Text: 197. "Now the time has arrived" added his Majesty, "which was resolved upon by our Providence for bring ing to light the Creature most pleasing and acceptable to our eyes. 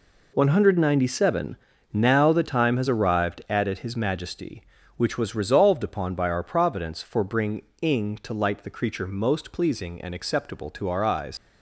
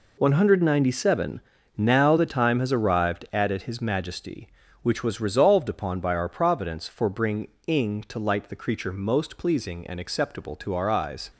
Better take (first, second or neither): second